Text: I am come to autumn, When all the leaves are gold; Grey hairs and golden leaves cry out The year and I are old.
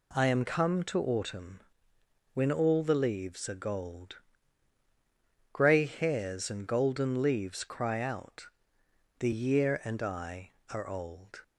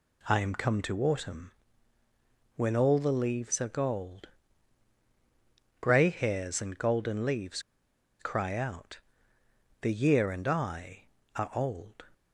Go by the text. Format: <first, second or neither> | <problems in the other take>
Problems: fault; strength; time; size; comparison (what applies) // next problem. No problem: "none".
first | pauses between "leaves" and "cry"; noticeable; at 7.5 s; 0.59 s long // pauses between "out" and "The"; noticeable; at 9.0 s; 0.80 s long; noticeable in the first